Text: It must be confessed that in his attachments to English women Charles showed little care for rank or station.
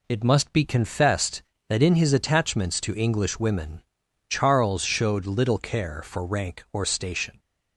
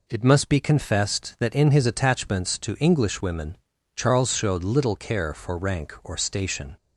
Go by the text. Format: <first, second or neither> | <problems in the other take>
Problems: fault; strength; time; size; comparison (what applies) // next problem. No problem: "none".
neither | pauses between "women" and "Charles"; the same in both